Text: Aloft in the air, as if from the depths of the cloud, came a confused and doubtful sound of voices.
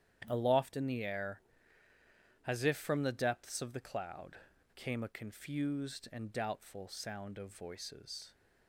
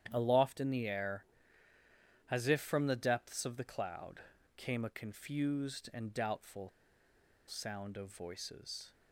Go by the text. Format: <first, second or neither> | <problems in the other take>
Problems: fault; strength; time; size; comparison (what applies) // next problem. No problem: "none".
first | starts louder than the rest; strong; until 1.1 s; 9.5 dB; strong in the first // pauses between "doubtful" and "sound"; noticeable; at 6.6 s; 0.78 s long